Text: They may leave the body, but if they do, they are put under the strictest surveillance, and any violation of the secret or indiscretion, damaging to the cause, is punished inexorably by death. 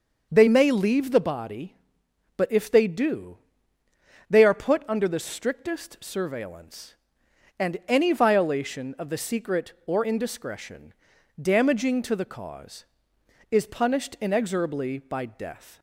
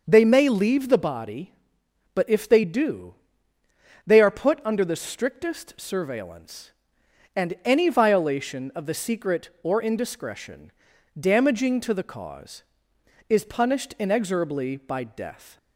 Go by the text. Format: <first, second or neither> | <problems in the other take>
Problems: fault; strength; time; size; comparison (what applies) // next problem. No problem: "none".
neither | starts louder than the rest; the same in both